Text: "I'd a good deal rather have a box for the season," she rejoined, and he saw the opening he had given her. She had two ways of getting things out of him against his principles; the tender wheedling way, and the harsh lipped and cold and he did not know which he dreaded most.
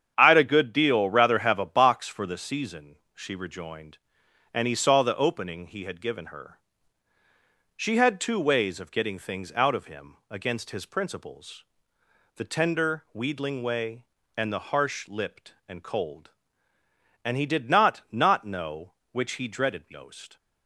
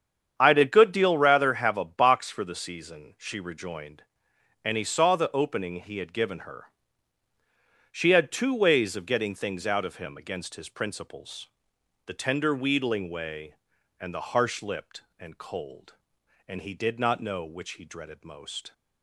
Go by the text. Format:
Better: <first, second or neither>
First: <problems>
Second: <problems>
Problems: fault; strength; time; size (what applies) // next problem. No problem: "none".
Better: second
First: starts louder than the rest; strong; until 1.1 s; 8 dB // says "not" twice; at 18.1 s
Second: starts louder than the rest; strong; until 1.3 s; 8 dB